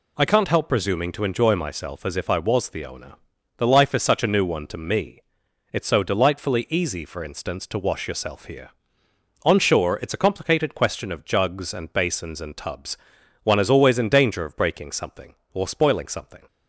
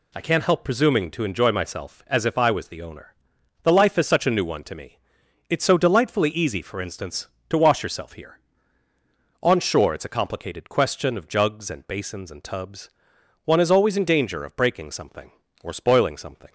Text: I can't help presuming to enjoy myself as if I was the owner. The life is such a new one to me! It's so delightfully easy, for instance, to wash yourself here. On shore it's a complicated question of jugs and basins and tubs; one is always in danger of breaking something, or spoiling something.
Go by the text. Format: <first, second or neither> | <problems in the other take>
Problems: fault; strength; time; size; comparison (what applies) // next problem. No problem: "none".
neither | none